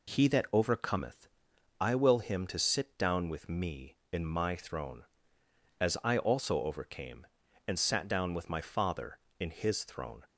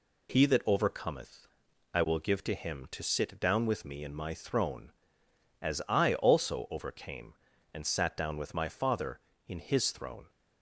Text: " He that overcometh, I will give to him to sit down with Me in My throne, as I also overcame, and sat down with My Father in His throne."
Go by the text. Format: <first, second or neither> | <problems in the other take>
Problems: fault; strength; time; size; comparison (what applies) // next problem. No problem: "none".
second | skips "give to"; at 2.2 s